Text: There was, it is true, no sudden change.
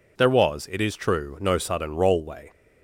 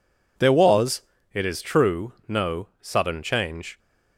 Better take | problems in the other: second | says "rollway" for "change"; at 1.9 s

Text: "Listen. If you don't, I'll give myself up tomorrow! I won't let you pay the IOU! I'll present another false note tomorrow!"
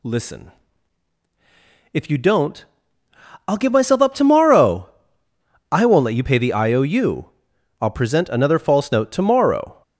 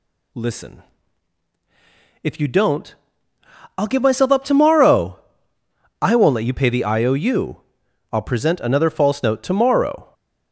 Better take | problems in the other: neither | none

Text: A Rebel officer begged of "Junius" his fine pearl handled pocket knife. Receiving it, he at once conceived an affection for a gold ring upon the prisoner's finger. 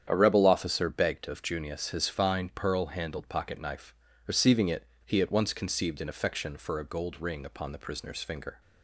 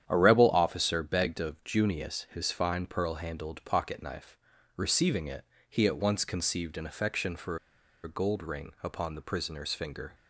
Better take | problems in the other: first | starts louder than the rest; strong; until 1.0 s; 9.5 dB; strong in the first // pauses between "for" and "a"; noticeable; at 7.5 s; 0.46 s long

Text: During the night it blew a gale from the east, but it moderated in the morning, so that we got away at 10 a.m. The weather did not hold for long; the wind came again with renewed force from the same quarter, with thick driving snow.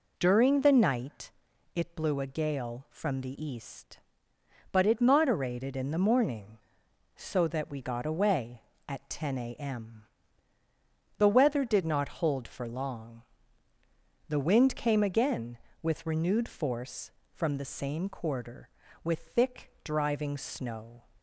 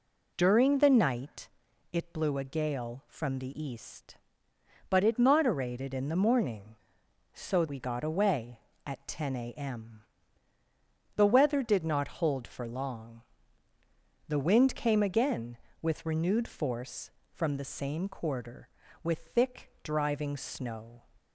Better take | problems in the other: first | pauses between "night" and "it"; at 1.4 s; 0.42 s long; also in the first // skips "that"; at 7.6 s

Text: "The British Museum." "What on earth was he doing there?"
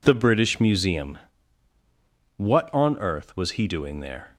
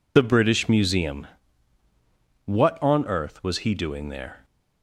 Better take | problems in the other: first | loses the start of "The"; at 0.1 s; 45 ms

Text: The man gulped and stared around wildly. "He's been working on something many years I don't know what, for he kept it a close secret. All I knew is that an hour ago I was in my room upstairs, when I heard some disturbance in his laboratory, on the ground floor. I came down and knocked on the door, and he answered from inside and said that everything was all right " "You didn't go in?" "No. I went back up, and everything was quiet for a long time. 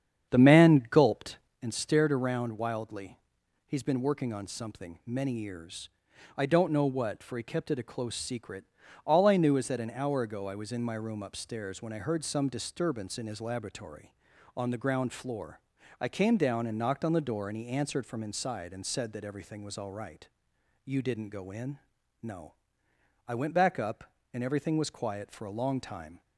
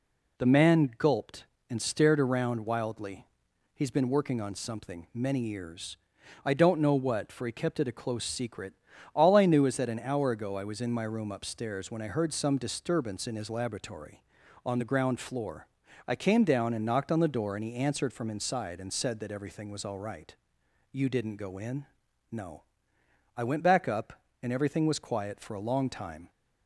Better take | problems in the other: second | starts louder than the rest; strong; until 1.6 s; 8.5 dB // pauses between "years" and "I"; noticeable; at 5.8 s; 0.50 s long; noticeable in the second

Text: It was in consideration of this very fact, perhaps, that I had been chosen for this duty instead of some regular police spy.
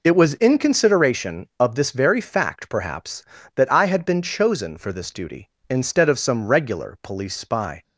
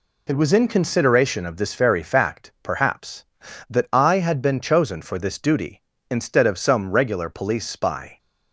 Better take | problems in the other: neither | none

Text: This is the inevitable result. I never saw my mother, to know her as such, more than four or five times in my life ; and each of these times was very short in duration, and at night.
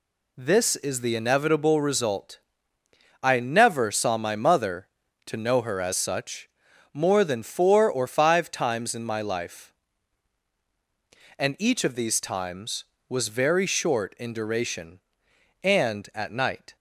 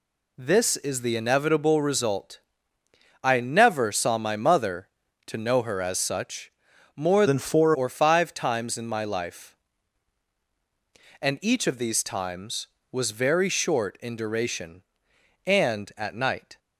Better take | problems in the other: first | changes voice from "than" to "four"; from 7.2 to 7.7 s; 0.5 s long

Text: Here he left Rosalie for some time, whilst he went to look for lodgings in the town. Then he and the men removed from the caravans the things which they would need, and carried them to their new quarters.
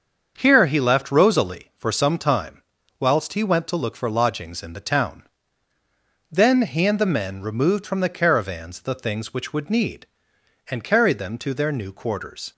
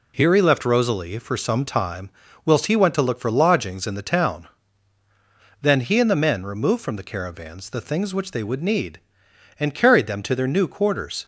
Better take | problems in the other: second | starts louder than the rest; until 1.3 s; 7 dB // skips "they"; at 9.5 s

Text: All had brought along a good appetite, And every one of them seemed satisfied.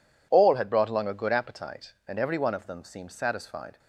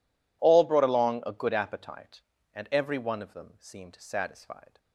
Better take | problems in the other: first | skips "had"; at 0.6 s

